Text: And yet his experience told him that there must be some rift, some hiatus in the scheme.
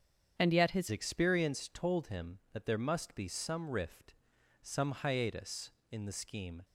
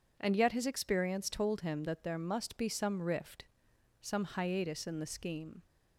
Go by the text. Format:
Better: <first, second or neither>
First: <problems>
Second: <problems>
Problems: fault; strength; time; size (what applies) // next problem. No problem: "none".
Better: second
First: starts louder than the rest; strong; until 1.4 s; 8 dB // changes voice at "experience"; from 0.9 s on; 5.7 s long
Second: none